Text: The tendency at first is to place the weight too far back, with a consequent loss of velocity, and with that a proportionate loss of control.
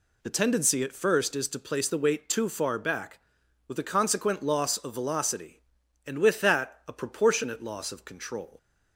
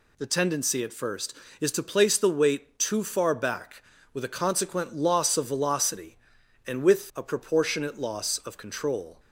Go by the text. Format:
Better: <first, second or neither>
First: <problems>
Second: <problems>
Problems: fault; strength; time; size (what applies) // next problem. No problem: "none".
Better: first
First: none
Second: skips "that"; at 7.1 s